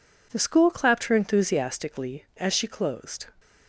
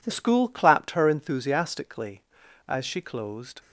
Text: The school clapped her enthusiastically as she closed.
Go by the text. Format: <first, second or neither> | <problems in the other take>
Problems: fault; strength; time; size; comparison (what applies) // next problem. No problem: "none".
first | changes voice at "school"; from 0.1 s on; 3.5 s long